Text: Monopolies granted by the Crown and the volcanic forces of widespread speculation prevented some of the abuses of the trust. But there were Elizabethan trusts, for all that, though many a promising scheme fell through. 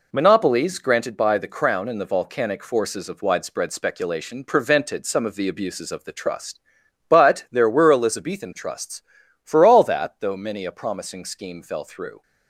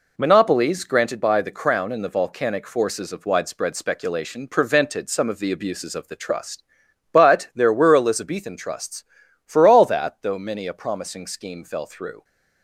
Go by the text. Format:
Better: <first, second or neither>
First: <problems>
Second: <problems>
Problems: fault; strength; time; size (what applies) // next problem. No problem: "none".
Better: neither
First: none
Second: none